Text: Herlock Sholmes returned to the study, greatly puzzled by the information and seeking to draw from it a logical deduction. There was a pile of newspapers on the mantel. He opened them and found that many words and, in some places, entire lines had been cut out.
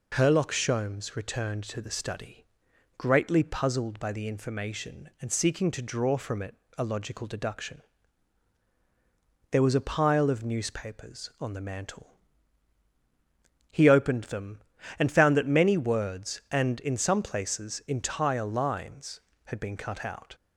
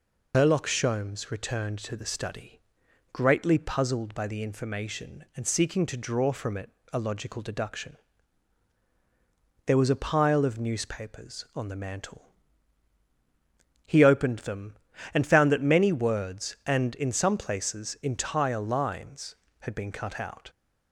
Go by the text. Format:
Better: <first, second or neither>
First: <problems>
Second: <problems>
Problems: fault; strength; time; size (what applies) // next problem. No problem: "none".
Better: first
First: pauses between "it" and "a"; slight; at 6.5 s; 0.24 s long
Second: loses the start of "Herlock"; at 0.3 s; 80 ms // pauses between "it" and "a"; slight; at 6.6 s; 0.24 s long